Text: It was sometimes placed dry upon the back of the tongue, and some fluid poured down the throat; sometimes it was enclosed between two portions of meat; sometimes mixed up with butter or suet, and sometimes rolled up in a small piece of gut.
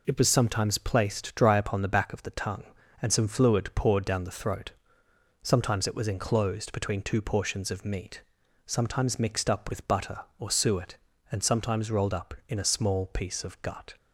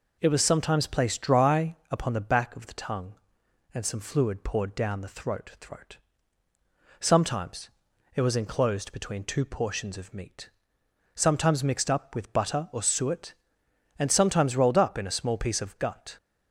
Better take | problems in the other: first | pauses between "dry" and "upon"; slight; at 1.7 s; 0.16 s long // says "throat" twice; at 5.6 s // pauses between "sometimes" and "it"; noticeable; at 7.6 s; 0.46 s long

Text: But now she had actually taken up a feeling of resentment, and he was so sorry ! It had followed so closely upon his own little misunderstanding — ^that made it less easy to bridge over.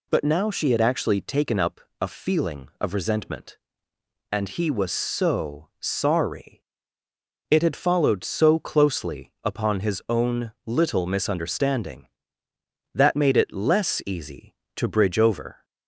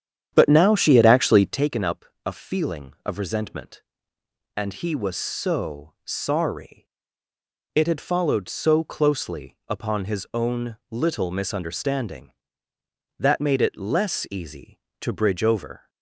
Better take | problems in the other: first | starts louder than the rest; strong; until 1.7 s; 9 dB // pauses between "up" and "a"; slight; at 2.0 s; 0.20 s long; slight in the first

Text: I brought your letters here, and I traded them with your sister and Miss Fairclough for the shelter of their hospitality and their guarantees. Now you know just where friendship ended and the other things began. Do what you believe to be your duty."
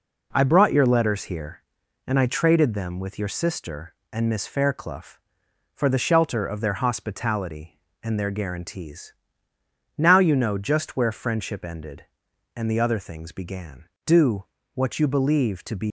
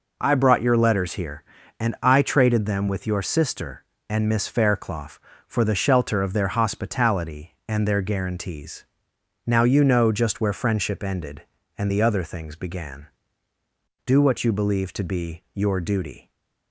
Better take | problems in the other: second | pauses between "Do" and "what"; slight; at 14.4 s; 0.29 s long // stops before "your duty"; at 15.8 s

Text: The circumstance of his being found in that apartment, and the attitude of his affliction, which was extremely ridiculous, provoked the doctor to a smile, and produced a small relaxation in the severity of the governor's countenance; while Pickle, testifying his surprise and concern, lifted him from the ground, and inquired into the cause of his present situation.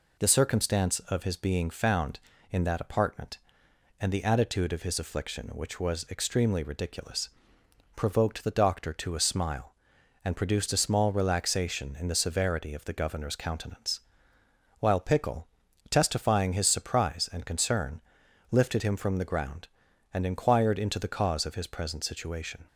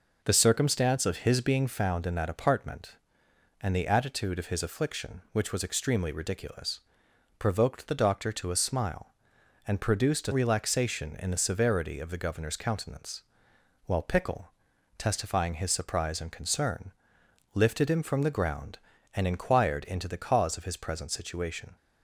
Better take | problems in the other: first | skips "small"; at 10.3 s

